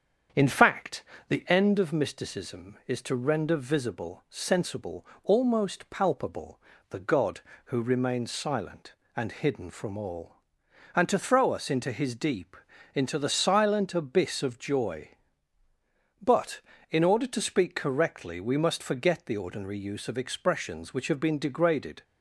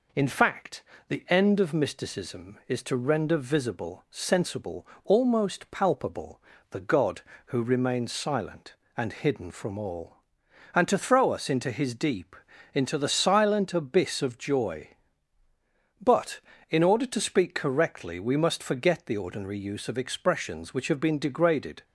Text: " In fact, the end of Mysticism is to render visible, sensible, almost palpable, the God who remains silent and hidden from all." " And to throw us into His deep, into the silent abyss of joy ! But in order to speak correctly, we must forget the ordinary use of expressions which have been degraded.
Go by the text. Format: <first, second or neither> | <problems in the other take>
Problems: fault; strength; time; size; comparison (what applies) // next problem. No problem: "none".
second | starts louder than the rest; strong; until 1.6 s; 7.5 dB